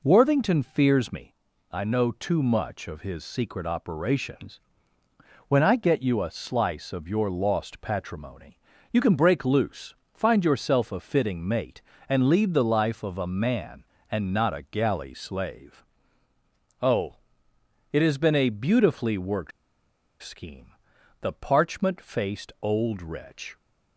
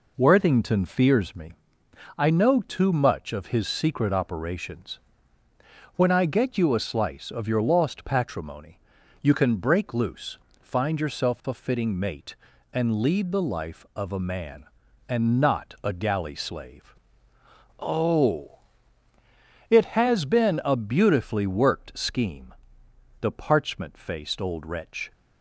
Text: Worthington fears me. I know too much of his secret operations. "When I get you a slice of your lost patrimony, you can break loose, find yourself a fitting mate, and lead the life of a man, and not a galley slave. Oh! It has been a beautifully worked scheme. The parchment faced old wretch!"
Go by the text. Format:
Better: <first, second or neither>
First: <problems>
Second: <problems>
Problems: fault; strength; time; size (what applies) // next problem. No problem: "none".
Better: second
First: pauses between "worked" and "scheme"; noticeable; at 19.5 s; 0.71 s long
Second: none